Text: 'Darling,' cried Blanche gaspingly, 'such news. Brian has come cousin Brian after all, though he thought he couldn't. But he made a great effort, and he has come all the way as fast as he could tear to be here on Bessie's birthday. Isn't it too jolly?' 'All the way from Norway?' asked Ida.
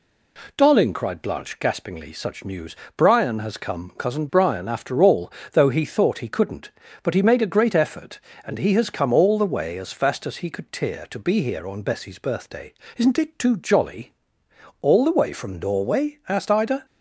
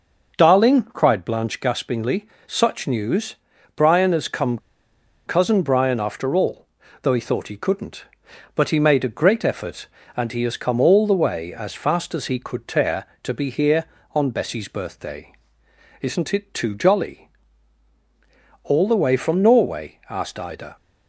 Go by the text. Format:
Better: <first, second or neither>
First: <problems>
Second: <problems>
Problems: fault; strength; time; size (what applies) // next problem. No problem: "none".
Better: first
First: none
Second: pauses between "come" and "cousin"; noticeable; at 4.5 s; 0.68 s long